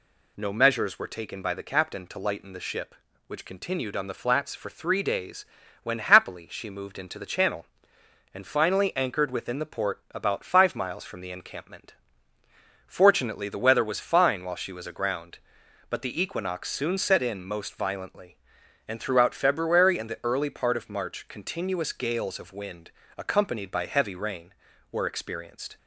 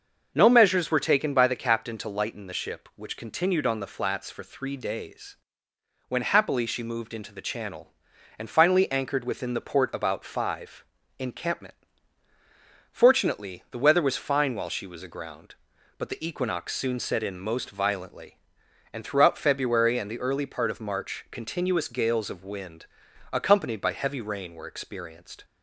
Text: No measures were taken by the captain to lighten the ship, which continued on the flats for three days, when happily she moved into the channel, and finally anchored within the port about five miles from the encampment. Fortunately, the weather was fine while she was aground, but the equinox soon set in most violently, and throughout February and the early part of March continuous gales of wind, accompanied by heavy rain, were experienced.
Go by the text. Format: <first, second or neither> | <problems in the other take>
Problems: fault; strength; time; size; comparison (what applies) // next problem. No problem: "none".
first | starts louder than the rest; until 1.3 s; 6.5 dB // skips "miles from the"; at 11.0 s